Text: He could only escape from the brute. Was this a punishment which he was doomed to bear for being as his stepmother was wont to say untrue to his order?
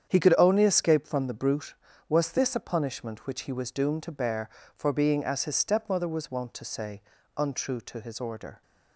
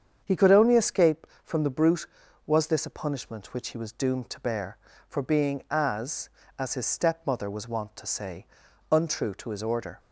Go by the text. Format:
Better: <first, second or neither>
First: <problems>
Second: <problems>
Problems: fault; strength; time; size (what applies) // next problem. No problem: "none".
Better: first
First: starts louder than the rest; strong; until 1.1 s; 8 dB // pauses between "say" and "untrue"; slight; at 7.0 s; 0.34 s long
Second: starts louder than the rest; strong; until 1.2 s; 7.5 dB // says "as" twice; at 6.5 s // pauses between "say" and "untrue"; at 8.4 s; 0.44 s long